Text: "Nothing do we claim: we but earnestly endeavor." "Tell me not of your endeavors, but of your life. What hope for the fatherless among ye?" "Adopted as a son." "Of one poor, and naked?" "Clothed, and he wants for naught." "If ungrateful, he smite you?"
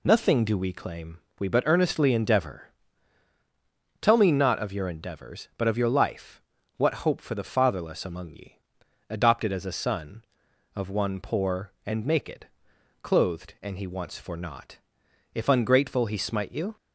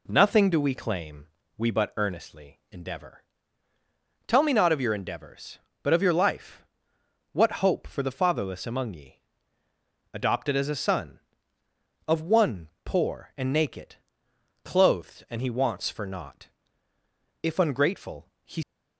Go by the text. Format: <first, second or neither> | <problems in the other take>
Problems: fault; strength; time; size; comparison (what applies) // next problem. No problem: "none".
first | pauses between "one" and "poor"; slight; at 12.6 s; 0.16 s long // stops before "smite you"; at 18.6 s